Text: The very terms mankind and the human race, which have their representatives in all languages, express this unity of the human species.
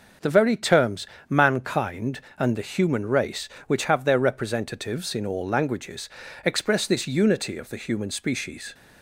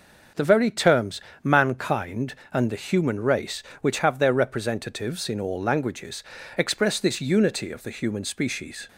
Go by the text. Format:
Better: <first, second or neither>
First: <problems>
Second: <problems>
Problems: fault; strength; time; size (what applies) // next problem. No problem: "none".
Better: neither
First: starts louder than the rest; until 1.4 s; 6.5 dB // pauses between "terms" and "mankind"; slight; at 1.0 s; 0.22 s long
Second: starts louder than the rest; until 1.5 s; 6.5 dB // pauses between "terms" and "mankind"; slight; at 1.2 s; 0.22 s long